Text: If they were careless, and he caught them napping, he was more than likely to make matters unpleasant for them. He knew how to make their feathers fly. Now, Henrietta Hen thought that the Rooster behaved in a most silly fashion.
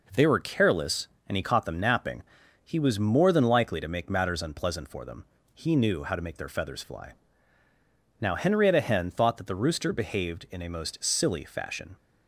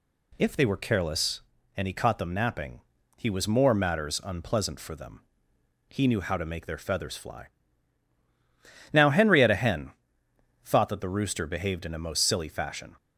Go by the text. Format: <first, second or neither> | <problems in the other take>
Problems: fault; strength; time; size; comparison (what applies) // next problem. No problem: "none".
first | skips "than likely to make"; at 3.7 s // pauses between "Hen" and "thought"; noticeable; at 9.9 s; 0.72 s long